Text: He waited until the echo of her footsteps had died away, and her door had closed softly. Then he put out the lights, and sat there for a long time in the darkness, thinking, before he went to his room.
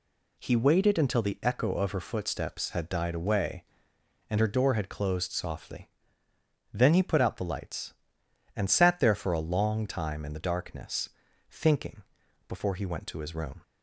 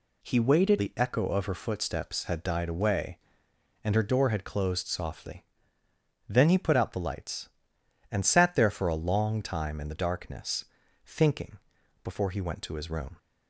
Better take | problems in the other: first | skips "until"; at 0.7 s

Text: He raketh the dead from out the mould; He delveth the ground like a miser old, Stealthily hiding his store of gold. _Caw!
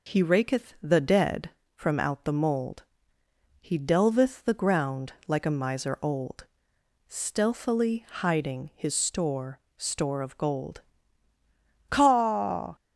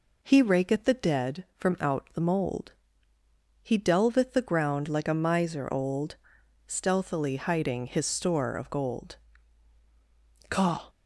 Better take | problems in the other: second | pauses between "ground" and "like"; slight; at 5.1 s; 0.16 s long // says "store" twice; at 9.7 s

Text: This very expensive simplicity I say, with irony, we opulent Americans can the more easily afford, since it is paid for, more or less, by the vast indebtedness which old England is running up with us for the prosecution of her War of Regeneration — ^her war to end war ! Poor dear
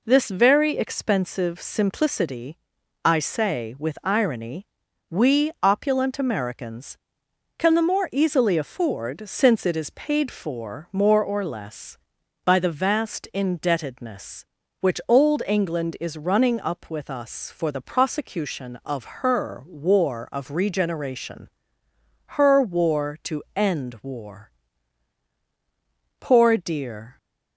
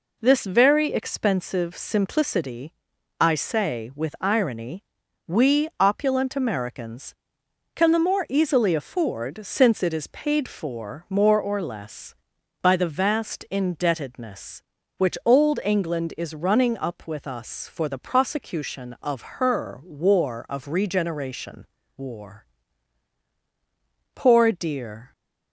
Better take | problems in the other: first | pauses between "simplicity" and "I"; noticeable; at 2.7 s; 0.48 s long; noticeable in the first // skips "her war to end"; at 21.8 s

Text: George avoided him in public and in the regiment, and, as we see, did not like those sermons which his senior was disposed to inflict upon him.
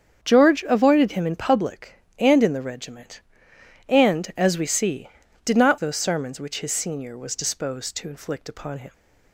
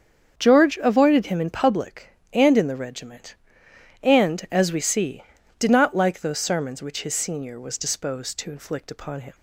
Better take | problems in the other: second | starts louder than the rest; strong; until 1.2 s; 7.5 dB; also in the second // skips "like"; at 5.7 s

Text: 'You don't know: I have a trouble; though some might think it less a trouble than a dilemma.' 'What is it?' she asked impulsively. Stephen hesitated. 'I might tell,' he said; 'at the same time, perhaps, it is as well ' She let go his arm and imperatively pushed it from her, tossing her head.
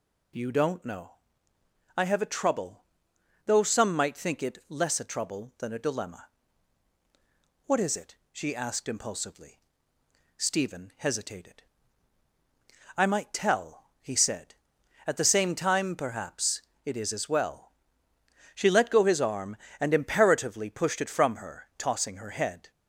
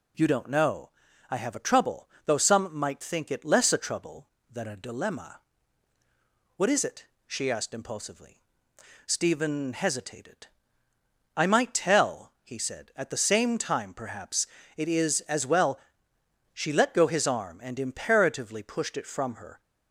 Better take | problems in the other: first | stops before "tossing her head"; at 19.5 s

